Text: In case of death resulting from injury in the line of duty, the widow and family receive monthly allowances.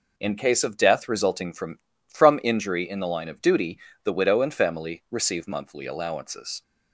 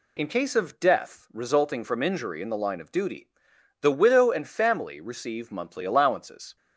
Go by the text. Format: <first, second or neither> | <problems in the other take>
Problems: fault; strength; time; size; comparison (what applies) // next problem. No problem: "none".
second | says "from" twice; at 2.0 s